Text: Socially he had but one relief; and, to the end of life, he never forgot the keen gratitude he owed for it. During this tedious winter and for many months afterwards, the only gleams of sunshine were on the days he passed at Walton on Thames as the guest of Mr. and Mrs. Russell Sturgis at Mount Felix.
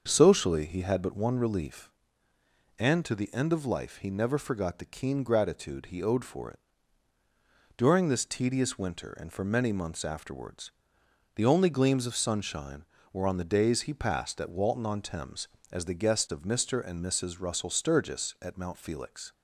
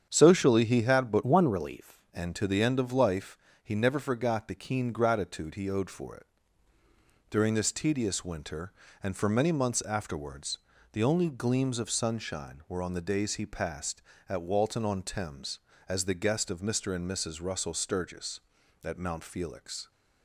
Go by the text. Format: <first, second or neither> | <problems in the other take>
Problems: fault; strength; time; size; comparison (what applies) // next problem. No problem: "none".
first | starts louder than the rest; strong; until 1.1 s; 8 dB; also in the first // changes voice from "one" to "relief"; from 1.2 to 2.0 s; 0.8 s long